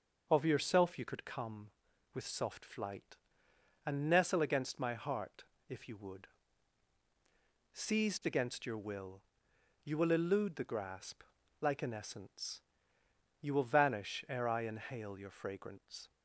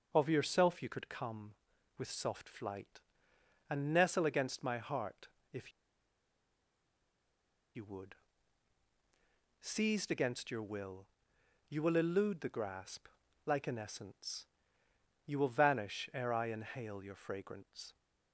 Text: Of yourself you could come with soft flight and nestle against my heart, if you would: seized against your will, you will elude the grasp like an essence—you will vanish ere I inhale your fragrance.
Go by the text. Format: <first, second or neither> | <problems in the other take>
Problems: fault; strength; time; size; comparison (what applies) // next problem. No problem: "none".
first | starts louder than the rest; noticeable; until 1.1 s; 6 dB; noticeable in the first // pauses between "if" and "you"; strong; at 5.7 s; 2.0 s long // pauses between "grasp" and "like"; at 13.0 s; 0.38 s long; also in the first